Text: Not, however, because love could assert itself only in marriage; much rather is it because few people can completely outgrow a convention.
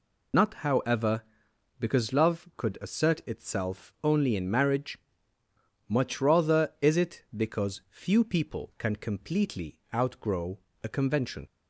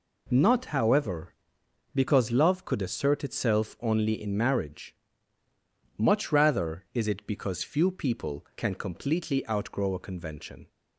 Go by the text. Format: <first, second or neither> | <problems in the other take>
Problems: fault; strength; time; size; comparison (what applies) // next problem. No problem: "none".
second | loses the start of "Not"; at 0.3 s; 65 ms // pauses between "completely" and "outgrow"; slight; at 9.7 s; 0.16 s long // pauses between "outgrow" and "a"; slight; at 10.5 s; 0.24 s long